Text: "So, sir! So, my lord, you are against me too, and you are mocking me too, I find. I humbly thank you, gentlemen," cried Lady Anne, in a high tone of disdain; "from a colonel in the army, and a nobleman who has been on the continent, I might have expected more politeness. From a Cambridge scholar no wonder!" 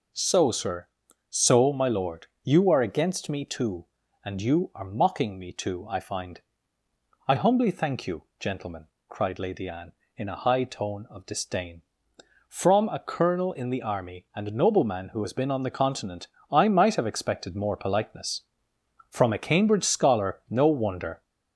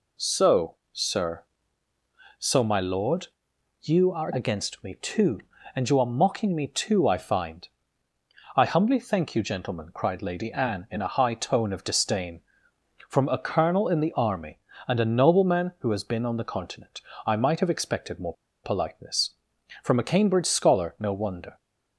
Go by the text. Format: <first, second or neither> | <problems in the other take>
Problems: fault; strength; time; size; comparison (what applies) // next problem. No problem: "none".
first | pauses between "more" and "politeness"; slight; at 18.3 s; 0.30 s long